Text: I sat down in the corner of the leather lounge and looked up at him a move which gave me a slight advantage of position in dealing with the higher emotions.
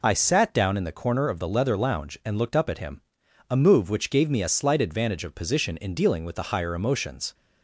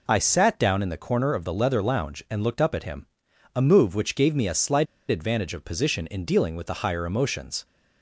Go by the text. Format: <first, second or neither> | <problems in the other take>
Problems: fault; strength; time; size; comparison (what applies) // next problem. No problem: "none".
first | pauses between "him" and "a"; noticeable; at 3.0 s; 0.48 s long; noticeable in the first // pauses between "slight" and "advantage"; slight; at 4.8 s; 0.23 s long